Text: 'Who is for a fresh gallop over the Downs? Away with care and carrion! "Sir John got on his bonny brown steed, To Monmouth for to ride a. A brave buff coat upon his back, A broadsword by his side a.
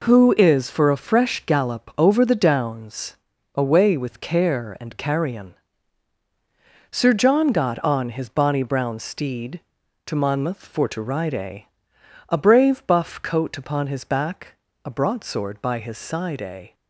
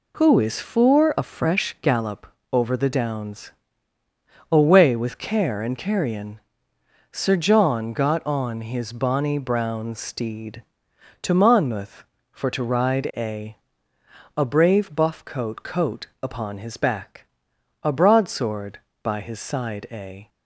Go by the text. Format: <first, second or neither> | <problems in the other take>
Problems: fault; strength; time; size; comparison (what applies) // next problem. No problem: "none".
first | pauses between "gallop" and "over"; slight; at 2.2 s; 0.24 s long // says "coat" twice; at 15.6 s